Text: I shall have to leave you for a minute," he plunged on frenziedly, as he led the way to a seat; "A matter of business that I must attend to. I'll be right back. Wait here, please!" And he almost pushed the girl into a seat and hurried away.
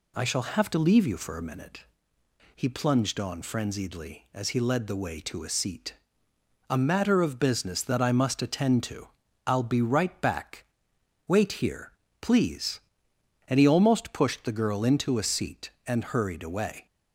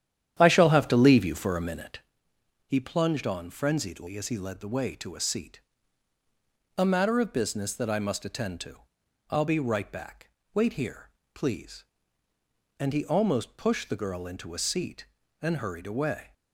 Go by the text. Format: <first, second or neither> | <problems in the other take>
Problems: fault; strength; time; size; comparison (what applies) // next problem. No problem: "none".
first | starts louder than the rest; strong; until 2.2 s; 10 dB